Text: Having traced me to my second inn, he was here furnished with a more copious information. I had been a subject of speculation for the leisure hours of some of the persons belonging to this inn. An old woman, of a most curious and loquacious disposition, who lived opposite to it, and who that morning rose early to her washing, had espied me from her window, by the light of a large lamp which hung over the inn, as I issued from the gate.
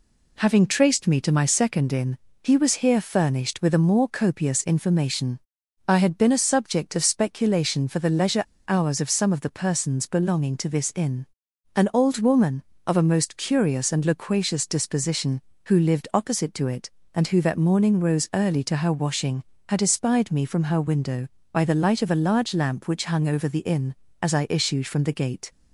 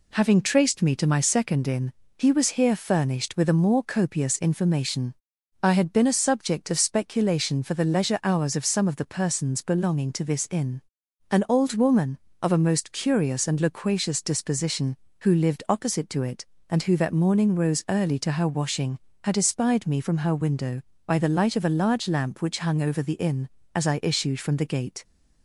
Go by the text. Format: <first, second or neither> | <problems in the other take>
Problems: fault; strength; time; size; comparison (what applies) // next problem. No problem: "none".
second | pauses between "leisure" and "hours"; slight; at 8.4 s; 0.25 s long